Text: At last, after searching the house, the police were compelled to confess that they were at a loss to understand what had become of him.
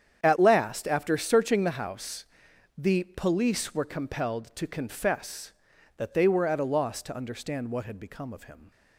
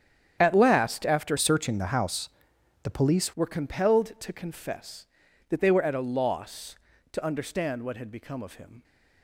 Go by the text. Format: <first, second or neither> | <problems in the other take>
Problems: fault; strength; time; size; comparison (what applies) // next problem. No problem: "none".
first | starts louder than the rest; strong; until 1.4 s; 8.5 dB; strong in the first // changes voice from "searching" to "police"; from 1.3 to 3.3 s; 2.0 s long